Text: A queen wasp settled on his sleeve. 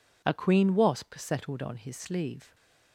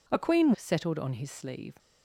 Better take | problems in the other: first | skips "wasp"; at 0.5 s

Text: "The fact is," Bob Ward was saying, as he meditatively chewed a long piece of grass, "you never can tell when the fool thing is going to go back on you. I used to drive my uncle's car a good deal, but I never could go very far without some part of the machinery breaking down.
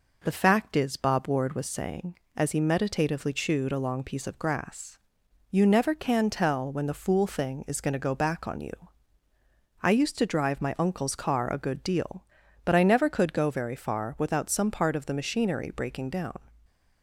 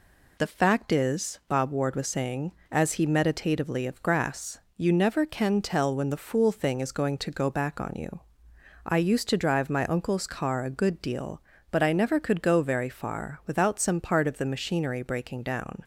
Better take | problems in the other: first | skips "chewed a long piece"; at 3.8 s

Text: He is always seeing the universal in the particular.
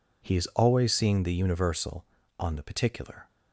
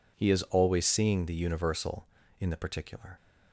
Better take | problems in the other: second | says "on" for "in"; at 2.3 s

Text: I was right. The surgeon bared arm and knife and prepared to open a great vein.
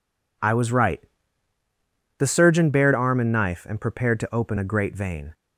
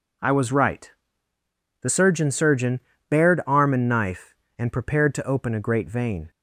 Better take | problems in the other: first | says "surgeon" twice; at 2.2 s

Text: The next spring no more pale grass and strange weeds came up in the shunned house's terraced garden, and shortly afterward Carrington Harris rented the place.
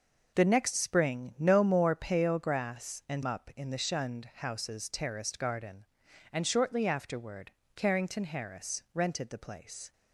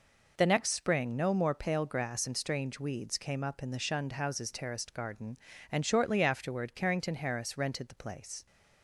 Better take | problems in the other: second | skips "strange weeds came"; at 3.2 s // pauses between "afterward" and "Carrington"; slight; at 7.5 s; 0.24 s long

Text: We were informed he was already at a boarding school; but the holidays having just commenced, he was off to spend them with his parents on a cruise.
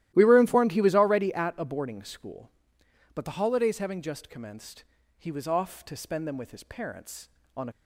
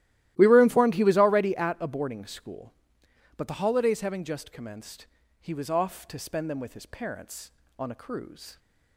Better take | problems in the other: second | starts louder than the rest; strong; until 1.1 s; 14 dB; strong in the second // stops before "cruise"; at 7.7 s

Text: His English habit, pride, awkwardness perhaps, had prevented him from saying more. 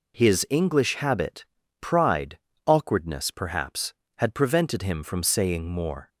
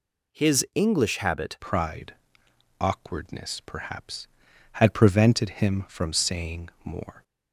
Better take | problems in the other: first | changes voice at "pride"; from 1.5 s on; 5.7 s long // pauses between "saying" and "more"; slight; at 6.6 s; 0.16 s long

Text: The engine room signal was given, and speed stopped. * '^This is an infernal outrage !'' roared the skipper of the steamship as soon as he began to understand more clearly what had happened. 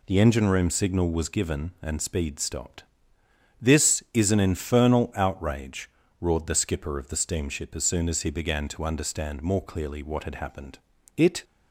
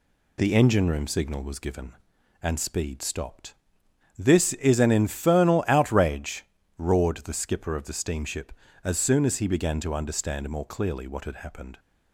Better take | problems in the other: second | goes on to say "It"; slight; from 11.1 s on; 0.28 s long

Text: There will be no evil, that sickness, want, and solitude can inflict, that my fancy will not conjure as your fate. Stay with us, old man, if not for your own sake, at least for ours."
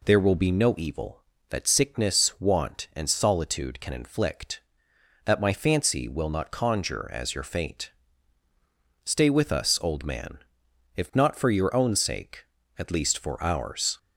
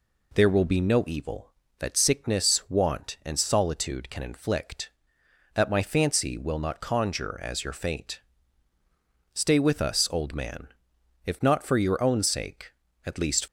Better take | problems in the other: first | stops before "for ours"; at 13.4 s

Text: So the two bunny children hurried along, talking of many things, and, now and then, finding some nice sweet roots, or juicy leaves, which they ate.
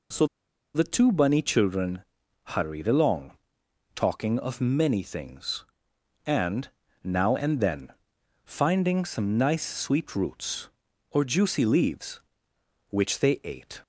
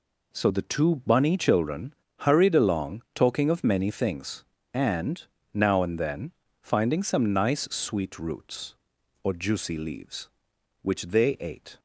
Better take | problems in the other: second | pauses between "So" and "the"; noticeable; at 0.2 s; 0.49 s long // pauses between "children" and "hurried"; at 2.0 s; 0.40 s long; slight in the second

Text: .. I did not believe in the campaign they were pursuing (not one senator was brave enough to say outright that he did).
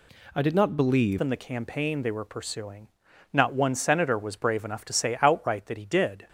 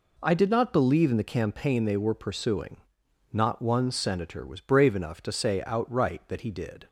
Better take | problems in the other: second | changes voice at "in"; from 1.1 s on; 5.1 s long

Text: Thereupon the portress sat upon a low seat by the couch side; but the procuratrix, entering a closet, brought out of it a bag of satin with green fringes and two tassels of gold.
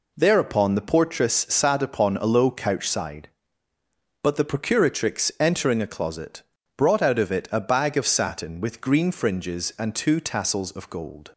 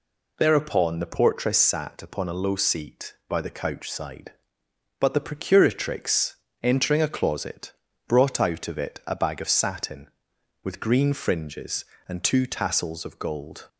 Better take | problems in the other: second | pauses between "portress" and "sat"; slight; at 1.3 s; 0.16 s long // skips "seat by the"; at 2.5 s

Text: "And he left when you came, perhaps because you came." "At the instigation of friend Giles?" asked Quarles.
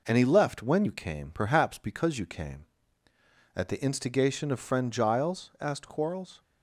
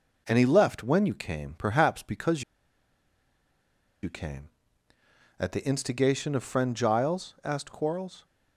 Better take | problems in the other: first | pauses between "because" and "you"; strong; at 2.4 s; 1.5 s long

